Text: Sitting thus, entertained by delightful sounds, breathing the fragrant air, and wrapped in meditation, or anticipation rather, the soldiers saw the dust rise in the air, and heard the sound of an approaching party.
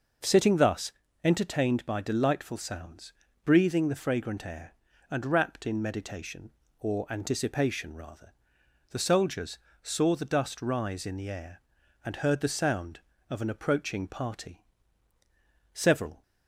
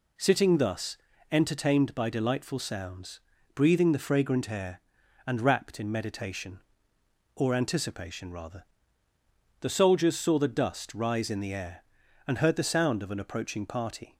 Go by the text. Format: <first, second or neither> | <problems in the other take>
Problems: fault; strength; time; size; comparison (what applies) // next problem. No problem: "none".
second | pauses between "soldiers" and "saw"; slight; at 9.5 s; 0.24 s long // goes on to say "Several"; slight; from 15.7 s on; 0.48 s long